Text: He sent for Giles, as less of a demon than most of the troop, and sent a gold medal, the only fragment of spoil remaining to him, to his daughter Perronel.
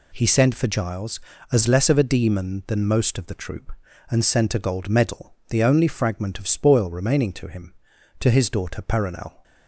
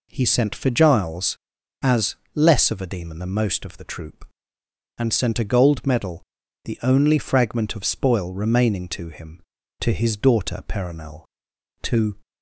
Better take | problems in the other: first | pauses between "as" and "less"; slight; at 2.1 s; 0.18 s long // goes on to say "To"; slight; from 11.8 s on; 0.36 s long

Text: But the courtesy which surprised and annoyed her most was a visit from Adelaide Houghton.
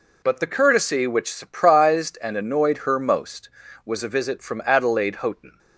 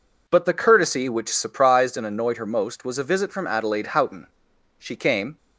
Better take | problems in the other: first | goes on to say "She came"; from 4.7 s on; 0.60 s long

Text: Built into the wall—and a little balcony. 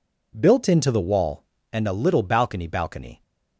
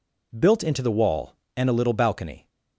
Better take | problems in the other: second | says "balcony" twice; at 2.6 s

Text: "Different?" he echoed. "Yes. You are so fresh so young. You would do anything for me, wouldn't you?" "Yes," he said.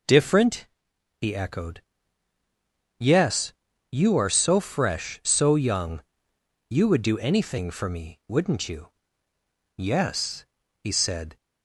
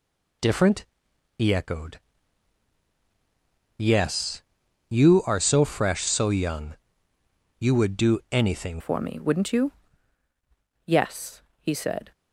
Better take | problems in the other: first | changes voice at "for"; from 8.7 s on; 3.4 s long

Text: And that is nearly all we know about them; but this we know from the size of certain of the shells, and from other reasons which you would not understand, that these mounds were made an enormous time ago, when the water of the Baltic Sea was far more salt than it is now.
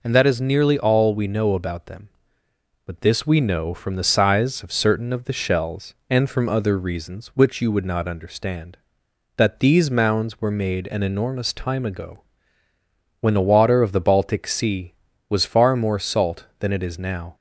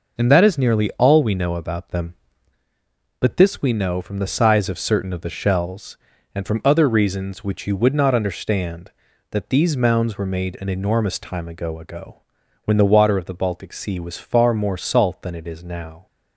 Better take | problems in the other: first | says "ago" twice; at 11.7 s

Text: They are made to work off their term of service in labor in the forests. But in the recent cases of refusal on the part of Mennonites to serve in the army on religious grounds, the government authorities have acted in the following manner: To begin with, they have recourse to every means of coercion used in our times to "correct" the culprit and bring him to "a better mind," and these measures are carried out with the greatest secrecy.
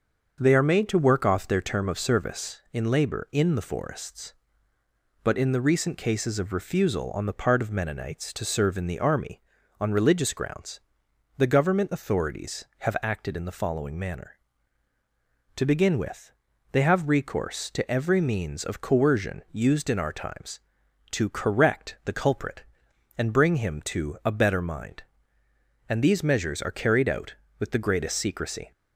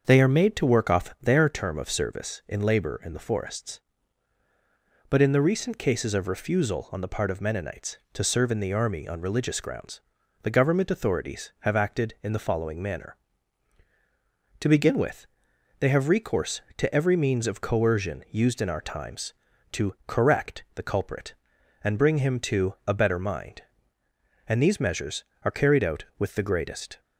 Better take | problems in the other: first | starts louder than the rest; until 1.0 s; 6.5 dB; also in the first // stops before "secrecy"; at 26.9 s

